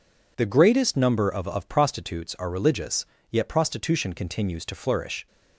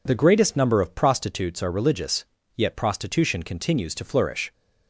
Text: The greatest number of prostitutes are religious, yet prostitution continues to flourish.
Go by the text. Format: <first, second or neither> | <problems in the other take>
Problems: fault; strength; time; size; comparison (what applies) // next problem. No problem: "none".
second | says "of" twice; at 1.4 s